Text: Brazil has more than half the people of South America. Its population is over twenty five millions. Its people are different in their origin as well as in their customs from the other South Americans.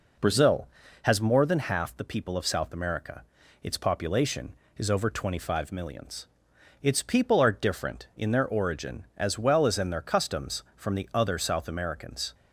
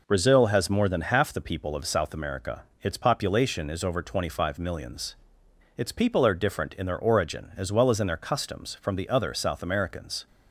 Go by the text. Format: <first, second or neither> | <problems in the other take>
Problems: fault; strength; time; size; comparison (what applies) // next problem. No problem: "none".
neither | none